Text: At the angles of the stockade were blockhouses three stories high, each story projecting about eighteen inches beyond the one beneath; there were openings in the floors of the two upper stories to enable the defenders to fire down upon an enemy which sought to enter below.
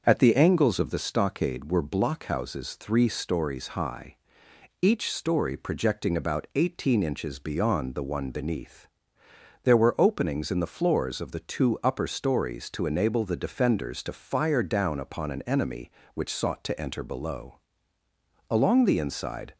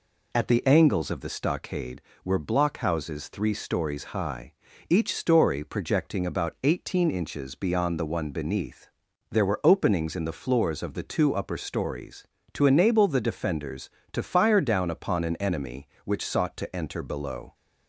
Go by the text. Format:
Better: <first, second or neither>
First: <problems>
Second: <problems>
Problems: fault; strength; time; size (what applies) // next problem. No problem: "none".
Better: second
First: starts louder than the rest; until 1.0 s; 6.5 dB // goes on to say "Along the inside"; noticeable; from 18.5 s on; 1.0 s long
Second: none